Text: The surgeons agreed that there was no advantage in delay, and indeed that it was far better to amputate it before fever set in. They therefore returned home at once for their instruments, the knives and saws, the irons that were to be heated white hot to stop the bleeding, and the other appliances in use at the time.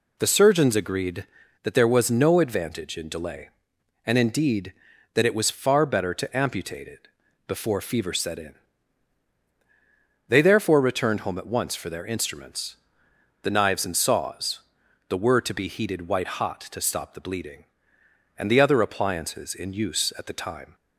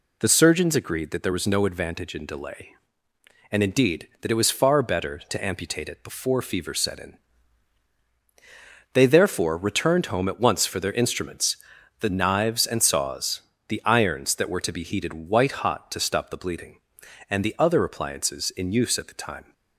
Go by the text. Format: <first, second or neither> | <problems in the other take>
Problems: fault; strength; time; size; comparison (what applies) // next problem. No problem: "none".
second | pauses between "it" and "before"; at 7.0 s; 0.40 s long // skips "irons that"; at 15.1 s